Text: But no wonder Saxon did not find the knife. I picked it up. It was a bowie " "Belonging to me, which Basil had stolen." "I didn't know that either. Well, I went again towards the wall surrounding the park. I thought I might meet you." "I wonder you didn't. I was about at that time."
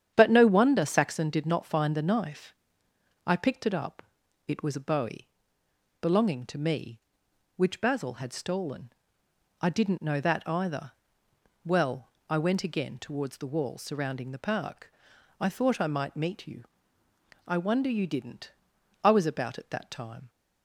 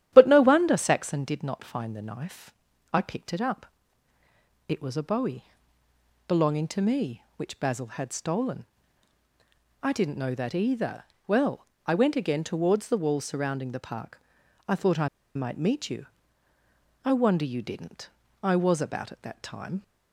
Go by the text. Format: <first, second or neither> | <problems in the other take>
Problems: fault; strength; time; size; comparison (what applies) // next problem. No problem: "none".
first | starts louder than the rest; strong; until 1.1 s; 12.5 dB; strong in the first // pauses between "I" and "might"; slight; at 15.0 s; 0.27 s long